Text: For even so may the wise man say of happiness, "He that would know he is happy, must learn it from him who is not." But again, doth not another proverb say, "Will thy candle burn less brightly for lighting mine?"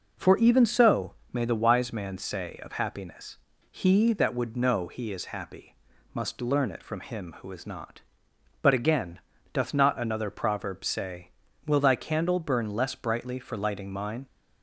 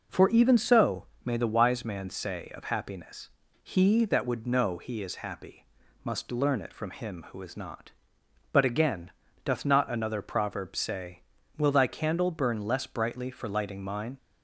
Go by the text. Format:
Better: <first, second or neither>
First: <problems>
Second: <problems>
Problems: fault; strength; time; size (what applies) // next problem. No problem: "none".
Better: neither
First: pauses between "so" and "may"; slight; at 1.1 s; 0.18 s long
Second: pauses between "so" and "may"; slight; at 1.0 s; 0.18 s long